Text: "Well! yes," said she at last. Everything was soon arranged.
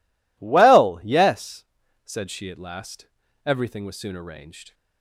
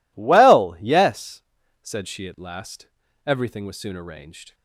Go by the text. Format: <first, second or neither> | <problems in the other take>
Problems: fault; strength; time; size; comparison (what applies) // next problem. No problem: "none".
neither | none